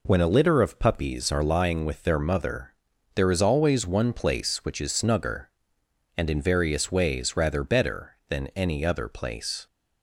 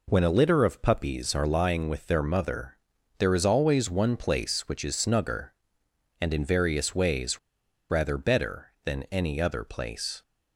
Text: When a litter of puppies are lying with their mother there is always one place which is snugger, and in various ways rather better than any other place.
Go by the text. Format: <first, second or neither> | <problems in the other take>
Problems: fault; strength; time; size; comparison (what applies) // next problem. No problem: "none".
first | pauses between "mother" and "there"; at 2.7 s; 0.42 s long; also in the first // pauses between "ways" and "rather"; noticeable; at 7.3 s; 0.50 s long